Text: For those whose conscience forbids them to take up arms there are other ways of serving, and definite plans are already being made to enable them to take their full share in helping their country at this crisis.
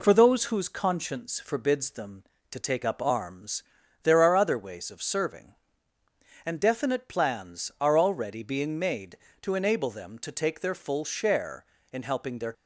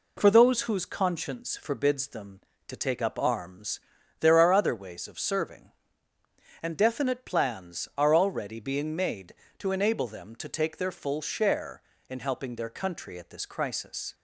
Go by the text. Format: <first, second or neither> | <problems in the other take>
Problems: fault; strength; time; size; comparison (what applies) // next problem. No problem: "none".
second | pauses between "arms" and "there"; at 3.6 s; 0.40 s long; also in the second // stops before "country at this crisis"; at 12.5 s